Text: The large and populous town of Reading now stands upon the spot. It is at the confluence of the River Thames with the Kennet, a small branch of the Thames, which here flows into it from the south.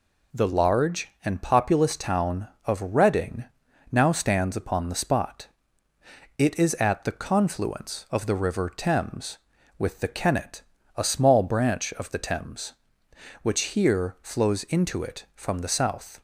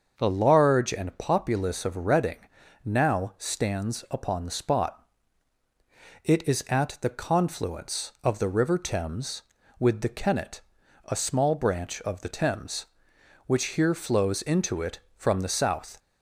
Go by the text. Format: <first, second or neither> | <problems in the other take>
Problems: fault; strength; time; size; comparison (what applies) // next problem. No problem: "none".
first | starts louder than the rest; until 1.2 s; 6.5 dB // skips "town"; at 1.8 s // pauses between "Reading" and "now"; noticeable; at 2.3 s; 0.46 s long; noticeable in the first